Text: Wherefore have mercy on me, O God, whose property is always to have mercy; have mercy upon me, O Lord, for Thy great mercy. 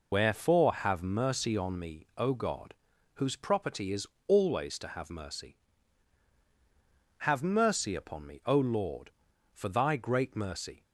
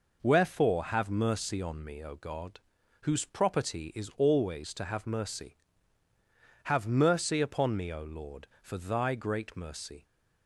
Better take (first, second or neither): second